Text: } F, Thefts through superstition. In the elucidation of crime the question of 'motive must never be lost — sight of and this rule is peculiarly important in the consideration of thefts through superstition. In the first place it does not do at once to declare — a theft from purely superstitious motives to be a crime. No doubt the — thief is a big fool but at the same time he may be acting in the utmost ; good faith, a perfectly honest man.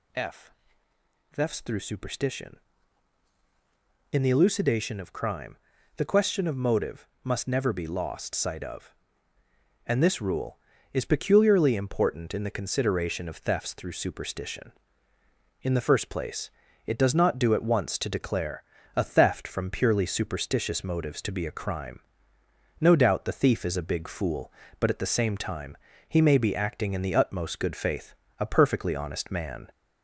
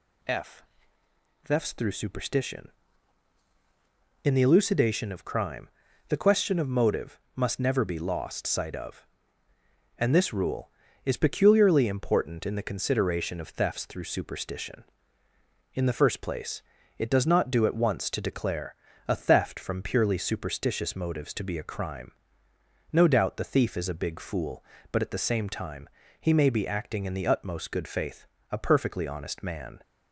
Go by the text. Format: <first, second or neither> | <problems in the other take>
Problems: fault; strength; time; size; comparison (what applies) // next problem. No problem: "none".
second | gets louder; slight; throughout; 2.5 dB // pauses between "crime" and "the"; at 5.5 s; 0.42 s long; also in the second // pauses between "motive" and "must"; slight; at 7.0 s; 0.16 s long; slight in the second // pauses between "place" and "it"; at 16.4 s; 0.38 s long; also in the second // pauses between "time" and "he"; slight; at 25.7 s; 0.32 s long; slight in the second